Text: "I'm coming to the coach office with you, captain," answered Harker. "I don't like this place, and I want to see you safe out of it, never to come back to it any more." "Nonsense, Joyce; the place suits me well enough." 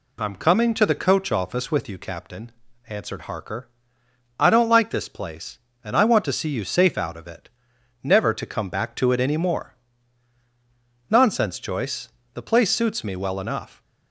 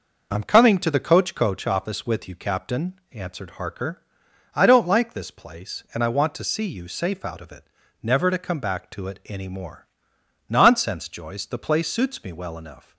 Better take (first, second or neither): first